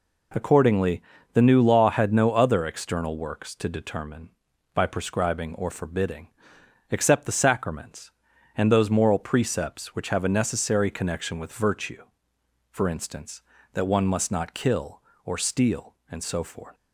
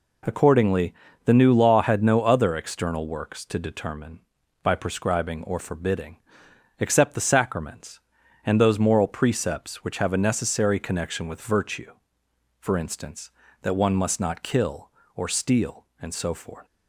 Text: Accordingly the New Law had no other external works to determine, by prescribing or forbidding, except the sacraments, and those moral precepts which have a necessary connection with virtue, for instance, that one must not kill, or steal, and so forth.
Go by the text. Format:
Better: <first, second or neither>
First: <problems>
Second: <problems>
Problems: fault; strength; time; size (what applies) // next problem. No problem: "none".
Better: neither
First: pauses between "Accordingly" and "the"; slight; at 1.0 s; 0.32 s long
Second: pauses between "Accordingly" and "the"; slight; at 0.9 s; 0.32 s long